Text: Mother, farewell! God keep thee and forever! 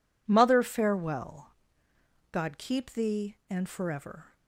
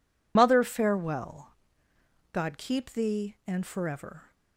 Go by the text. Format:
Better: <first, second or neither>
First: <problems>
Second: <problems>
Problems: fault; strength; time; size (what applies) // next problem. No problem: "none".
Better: first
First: none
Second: loses the start of "Mother"; at 0.3 s; 70 ms